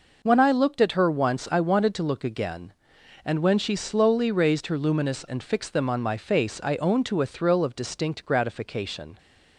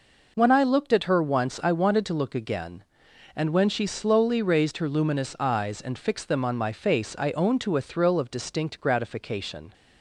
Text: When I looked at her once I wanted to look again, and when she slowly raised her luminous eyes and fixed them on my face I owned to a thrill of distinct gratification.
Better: second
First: skips "eyes"; at 5.2 s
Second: none

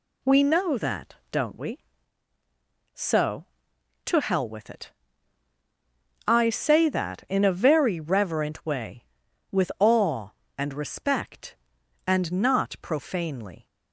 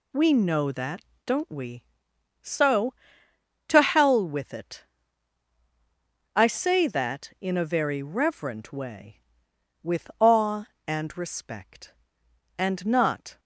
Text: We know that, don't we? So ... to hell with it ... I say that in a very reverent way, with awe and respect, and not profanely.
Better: first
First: none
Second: stops before "profanely"; at 13.3 s

